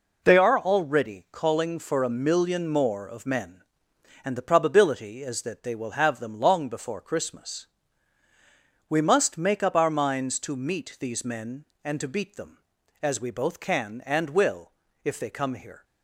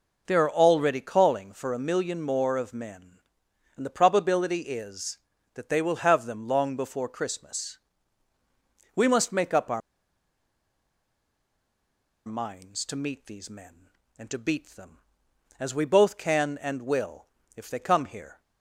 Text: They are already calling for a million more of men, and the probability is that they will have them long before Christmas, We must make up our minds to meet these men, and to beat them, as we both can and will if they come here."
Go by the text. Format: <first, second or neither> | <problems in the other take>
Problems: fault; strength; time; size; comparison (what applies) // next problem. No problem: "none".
first | pauses between "our" and "minds"; strong; at 9.8 s; 2.4 s long // pauses between "will" and "if"; slight; at 17.2 s; 0.28 s long; slight in the first